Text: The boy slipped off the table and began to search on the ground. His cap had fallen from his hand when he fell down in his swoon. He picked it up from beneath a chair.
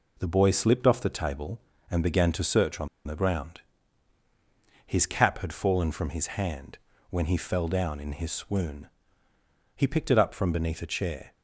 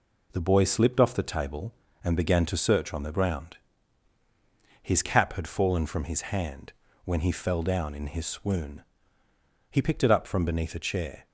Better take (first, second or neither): second